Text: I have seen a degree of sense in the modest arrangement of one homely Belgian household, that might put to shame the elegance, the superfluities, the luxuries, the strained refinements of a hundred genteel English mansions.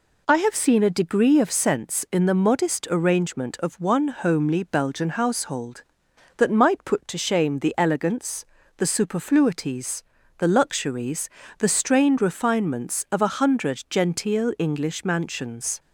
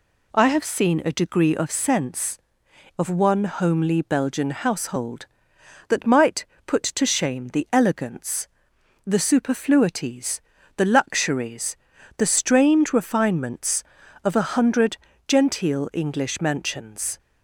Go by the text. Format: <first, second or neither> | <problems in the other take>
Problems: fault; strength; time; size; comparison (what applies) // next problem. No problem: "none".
first | skips "in the modest arrangement"; at 2.6 s // pauses between "might" and "put"; slight; at 6.4 s; 0.20 s long // pauses between "hundred" and "genteel"; slight; at 14.9 s; 0.30 s long